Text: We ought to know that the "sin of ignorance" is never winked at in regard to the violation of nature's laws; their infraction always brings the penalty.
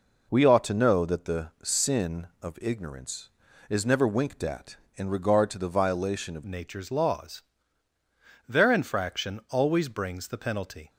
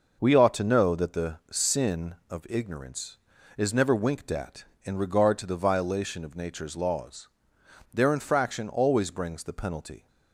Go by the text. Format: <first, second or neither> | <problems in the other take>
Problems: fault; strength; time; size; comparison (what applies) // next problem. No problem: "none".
second | changes voice at "nature's"; from 6.4 s on; 4.4 s long